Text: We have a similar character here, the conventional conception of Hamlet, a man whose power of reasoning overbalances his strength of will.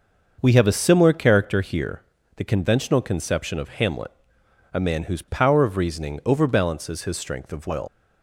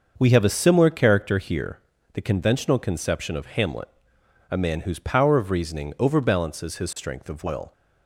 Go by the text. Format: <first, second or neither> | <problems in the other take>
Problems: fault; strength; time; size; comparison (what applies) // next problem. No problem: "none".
second | starts louder than the rest; noticeable; until 1.4 s; 6 dB; noticeable in the second // leaves "will" unfinished; at 7.8 s; 70 ms